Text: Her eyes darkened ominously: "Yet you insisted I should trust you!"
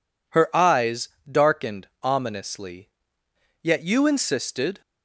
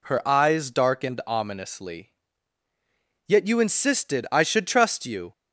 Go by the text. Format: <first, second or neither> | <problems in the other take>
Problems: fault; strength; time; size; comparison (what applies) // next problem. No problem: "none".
second | pauses between "eyes" and "darkened"; slight; at 1.0 s; 0.22 s long // pauses between "darkened" and "ominously"; slight; at 1.8 s; 0.16 s long // stops before "I should trust you"; at 4.8 s